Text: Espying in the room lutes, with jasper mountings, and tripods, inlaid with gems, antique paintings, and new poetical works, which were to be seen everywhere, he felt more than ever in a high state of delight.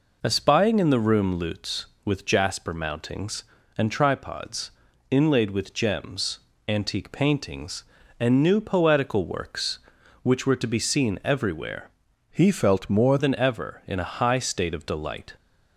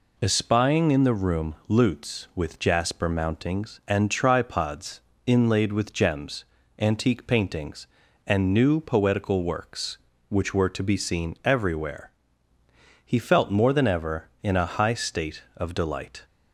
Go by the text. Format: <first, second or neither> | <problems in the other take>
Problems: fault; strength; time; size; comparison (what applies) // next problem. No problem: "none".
second | changes voice from "he" to "more"; from 12.2 to 13.1 s; 0.9 s long